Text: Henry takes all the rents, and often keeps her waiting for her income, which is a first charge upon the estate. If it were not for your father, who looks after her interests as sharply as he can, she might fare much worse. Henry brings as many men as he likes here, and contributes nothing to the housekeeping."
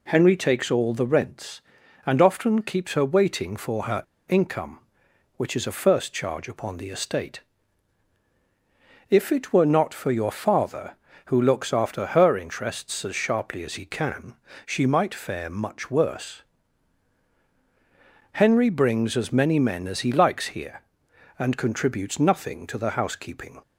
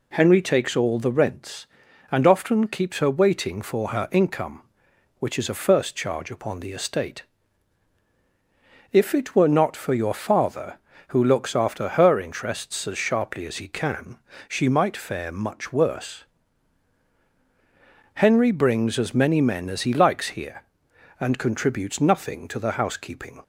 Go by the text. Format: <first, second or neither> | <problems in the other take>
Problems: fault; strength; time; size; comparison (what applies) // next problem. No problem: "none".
second | pauses between "her" and "income"; slight; at 4.0 s; 0.24 s long